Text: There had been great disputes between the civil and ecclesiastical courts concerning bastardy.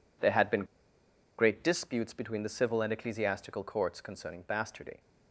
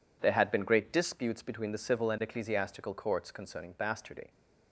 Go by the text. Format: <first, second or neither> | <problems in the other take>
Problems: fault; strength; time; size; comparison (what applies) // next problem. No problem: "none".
second | pauses between "been" and "great"; noticeable; at 0.6 s; 0.74 s long